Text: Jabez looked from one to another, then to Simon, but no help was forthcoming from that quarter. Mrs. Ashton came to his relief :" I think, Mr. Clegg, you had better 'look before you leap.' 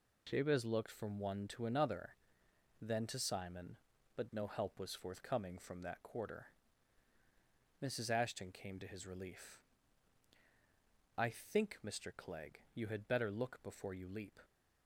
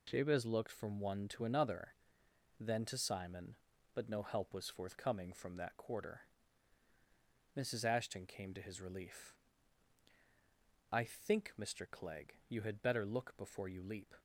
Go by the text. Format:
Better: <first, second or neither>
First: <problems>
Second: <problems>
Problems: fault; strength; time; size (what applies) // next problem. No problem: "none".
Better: neither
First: none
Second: none